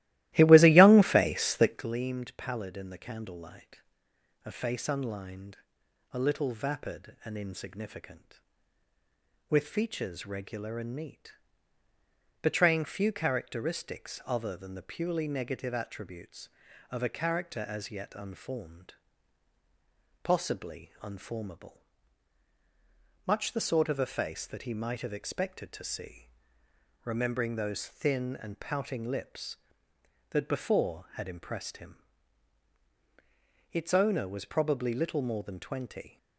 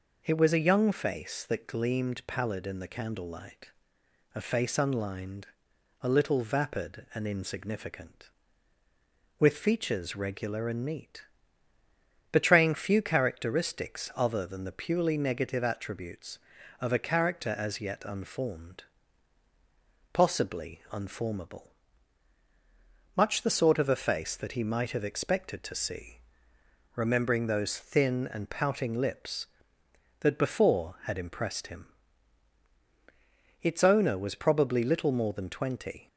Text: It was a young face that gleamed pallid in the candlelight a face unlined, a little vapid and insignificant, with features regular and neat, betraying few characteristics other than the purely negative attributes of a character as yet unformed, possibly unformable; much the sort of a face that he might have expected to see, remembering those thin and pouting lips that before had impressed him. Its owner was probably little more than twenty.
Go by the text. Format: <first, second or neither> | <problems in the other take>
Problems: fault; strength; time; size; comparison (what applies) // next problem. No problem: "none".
second | starts louder than the rest; strong; until 1.9 s; 16.5 dB // pauses between "candlelight" and "a"; noticeable; at 3.8 s; 0.64 s long; noticeable in the second